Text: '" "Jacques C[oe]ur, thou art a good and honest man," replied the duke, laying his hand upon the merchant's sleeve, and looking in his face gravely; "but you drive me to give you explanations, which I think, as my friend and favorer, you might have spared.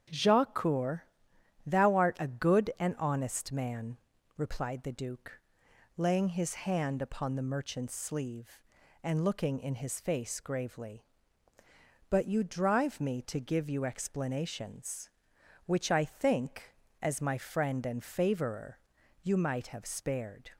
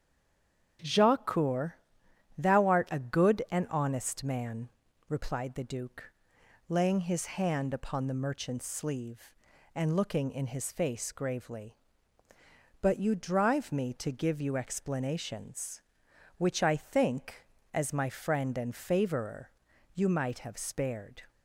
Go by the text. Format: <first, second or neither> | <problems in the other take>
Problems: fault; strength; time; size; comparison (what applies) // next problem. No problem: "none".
first | stays silent before the first word; slight; until 0.7 s; 0.7 s long // starts louder than the rest; strong; until 2.4 s; 8 dB; strong in the first